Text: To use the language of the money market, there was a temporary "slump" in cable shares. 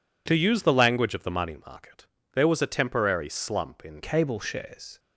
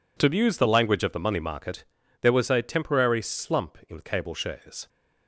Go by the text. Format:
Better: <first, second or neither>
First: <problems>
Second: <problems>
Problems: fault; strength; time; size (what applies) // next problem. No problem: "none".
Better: second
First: changes voice at "cable"; from 4.0 s on; 0.9 s long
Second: none